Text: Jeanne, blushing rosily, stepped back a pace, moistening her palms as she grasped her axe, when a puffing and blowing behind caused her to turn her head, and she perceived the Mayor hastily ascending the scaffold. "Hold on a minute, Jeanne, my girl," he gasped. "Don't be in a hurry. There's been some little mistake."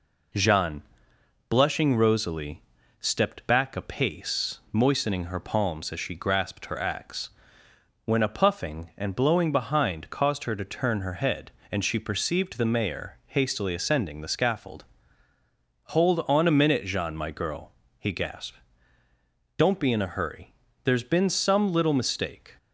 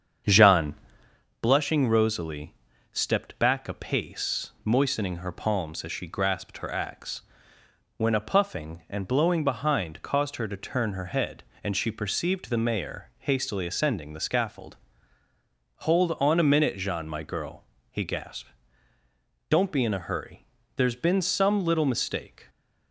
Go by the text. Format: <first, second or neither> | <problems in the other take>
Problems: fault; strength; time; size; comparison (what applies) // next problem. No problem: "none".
first | starts louder than the rest; strong; until 1.2 s; 7.5 dB